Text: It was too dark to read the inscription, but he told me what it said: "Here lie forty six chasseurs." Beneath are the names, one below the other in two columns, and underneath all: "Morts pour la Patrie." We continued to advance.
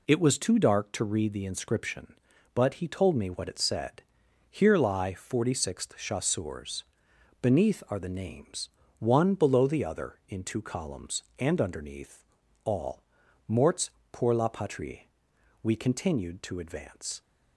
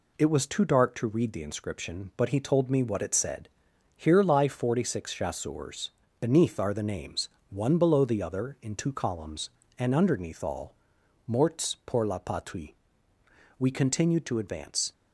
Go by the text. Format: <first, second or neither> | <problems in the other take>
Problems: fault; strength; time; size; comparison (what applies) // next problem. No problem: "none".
second | says "sixth" for "six"; at 5.5 s // pauses between "underneath" and "all"; at 12.2 s; 0.40 s long // pauses between "Morts" and "pour"; slight; at 13.9 s; 0.20 s long